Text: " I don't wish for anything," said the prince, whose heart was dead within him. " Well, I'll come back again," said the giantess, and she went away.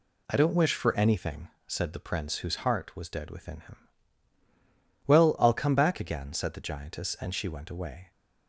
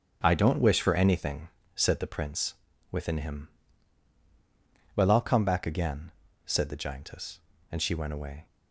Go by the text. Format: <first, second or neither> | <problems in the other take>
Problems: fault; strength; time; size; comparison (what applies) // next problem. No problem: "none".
first | skips "whose heart was dead"; at 2.7 s